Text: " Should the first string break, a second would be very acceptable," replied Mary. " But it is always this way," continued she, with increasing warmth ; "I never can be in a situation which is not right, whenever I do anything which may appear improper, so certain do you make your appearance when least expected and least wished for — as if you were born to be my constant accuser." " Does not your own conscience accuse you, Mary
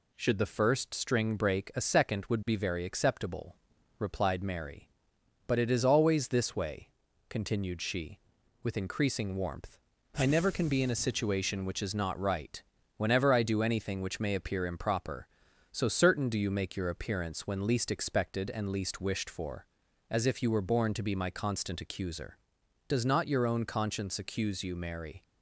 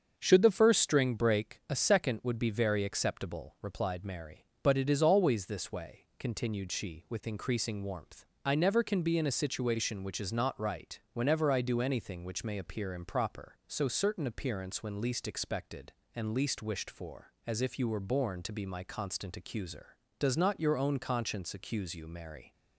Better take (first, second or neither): first